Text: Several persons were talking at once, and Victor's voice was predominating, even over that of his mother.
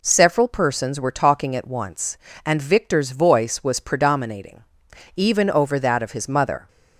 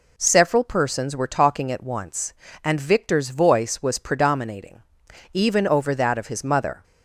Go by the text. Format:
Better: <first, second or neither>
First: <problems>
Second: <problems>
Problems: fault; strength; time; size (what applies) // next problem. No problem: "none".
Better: neither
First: none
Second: none